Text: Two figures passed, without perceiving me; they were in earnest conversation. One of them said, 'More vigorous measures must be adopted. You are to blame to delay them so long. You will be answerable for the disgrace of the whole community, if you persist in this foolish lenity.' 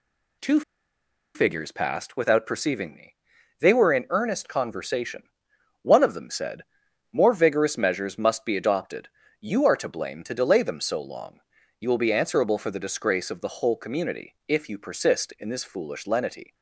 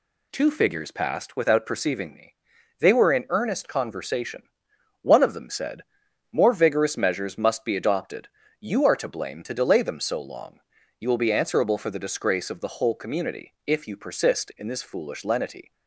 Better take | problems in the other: second | pauses between "Two" and "figures"; noticeable; at 0.6 s; 0.74 s long

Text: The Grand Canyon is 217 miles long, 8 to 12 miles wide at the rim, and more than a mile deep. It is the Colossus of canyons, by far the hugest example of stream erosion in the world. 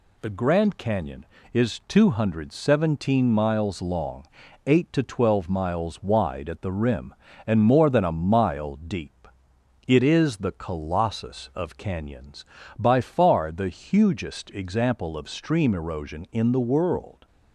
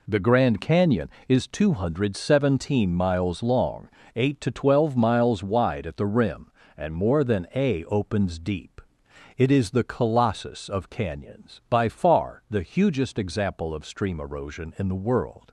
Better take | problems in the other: first | says "opens" for "mile"; at 7.8 s

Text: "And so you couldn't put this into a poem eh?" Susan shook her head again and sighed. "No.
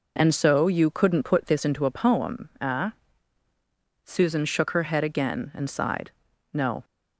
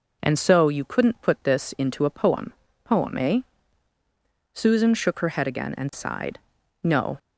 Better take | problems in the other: first | says "poem" twice; at 2.8 s

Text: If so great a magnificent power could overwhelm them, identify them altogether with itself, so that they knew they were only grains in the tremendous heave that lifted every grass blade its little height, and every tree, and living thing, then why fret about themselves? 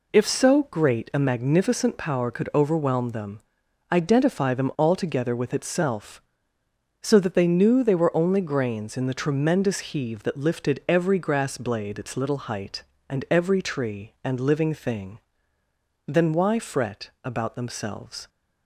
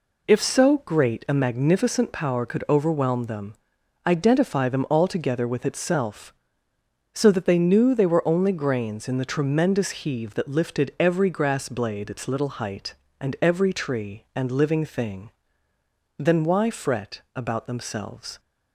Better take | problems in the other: neither | pauses between "fret" and "about"; slight; the same in both

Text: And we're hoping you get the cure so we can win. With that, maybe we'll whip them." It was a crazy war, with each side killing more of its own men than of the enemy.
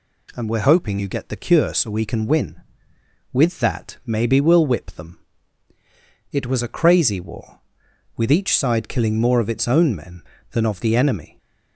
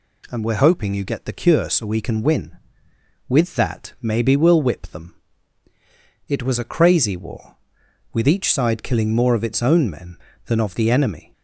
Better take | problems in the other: neither | none

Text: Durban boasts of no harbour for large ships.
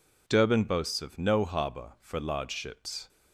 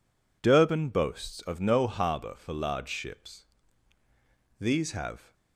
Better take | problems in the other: first | goes on to say "These have"; noticeable; from 4.6 s on; 0.72 s long

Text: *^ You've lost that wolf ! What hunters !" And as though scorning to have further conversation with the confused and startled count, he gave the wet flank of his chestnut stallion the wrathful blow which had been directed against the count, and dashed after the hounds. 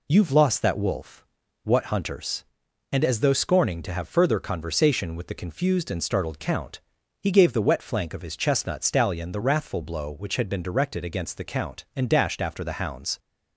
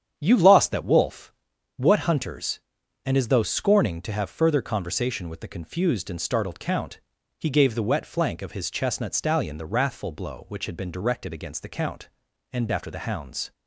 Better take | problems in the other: first | starts louder than the rest; strong; until 1.1 s; 9 dB // skips "dashed"; at 12.6 s

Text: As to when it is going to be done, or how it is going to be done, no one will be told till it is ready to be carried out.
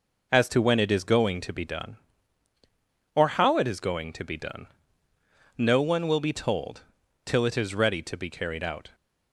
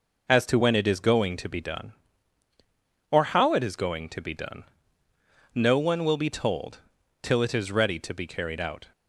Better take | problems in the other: neither | pauses between "told" and "till"; noticeable; the same in both

